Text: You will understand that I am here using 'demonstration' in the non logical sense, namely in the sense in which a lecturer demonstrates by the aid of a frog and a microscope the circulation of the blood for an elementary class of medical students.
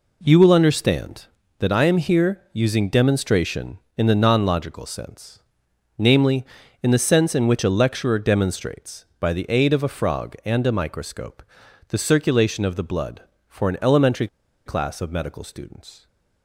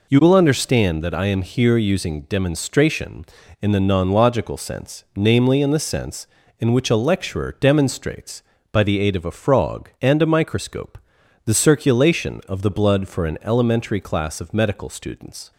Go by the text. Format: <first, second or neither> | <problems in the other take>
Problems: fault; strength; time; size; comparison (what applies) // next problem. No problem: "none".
second | pauses between "microscope" and "the"; noticeable; at 11.4 s; 0.46 s long; noticeable in the second // pauses between "elementary" and "class"; at 14.2 s; 0.38 s long